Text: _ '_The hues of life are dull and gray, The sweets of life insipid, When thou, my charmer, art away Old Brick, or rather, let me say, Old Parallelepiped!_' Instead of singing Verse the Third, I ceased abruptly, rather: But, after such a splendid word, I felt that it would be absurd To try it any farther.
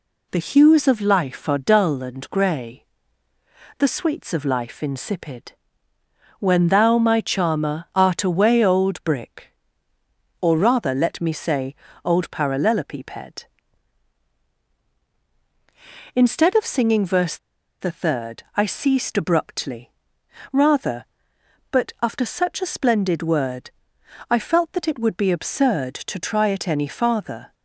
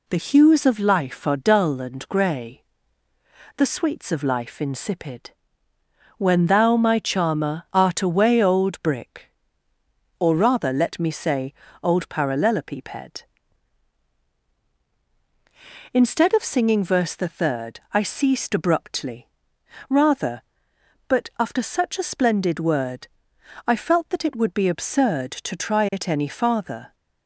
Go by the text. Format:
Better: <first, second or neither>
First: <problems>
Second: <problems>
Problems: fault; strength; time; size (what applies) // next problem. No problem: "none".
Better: second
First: pauses between "Verse" and "the"; at 17.3 s; 0.42 s long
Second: none